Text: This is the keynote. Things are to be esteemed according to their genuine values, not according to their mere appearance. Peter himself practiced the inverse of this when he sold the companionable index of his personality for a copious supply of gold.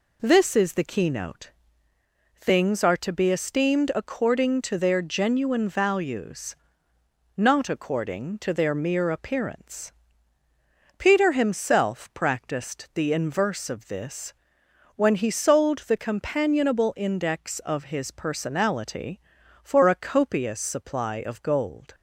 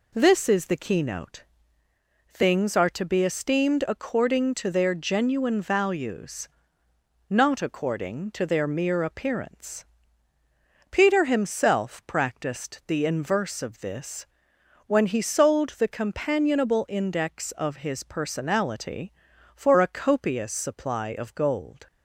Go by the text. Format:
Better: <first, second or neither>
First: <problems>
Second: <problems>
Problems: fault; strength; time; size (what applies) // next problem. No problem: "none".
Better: neither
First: pauses between "this" and "when"; noticeable; at 14.3 s; 0.62 s long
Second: pauses between "this" and "when"; noticeable; at 14.2 s; 0.60 s long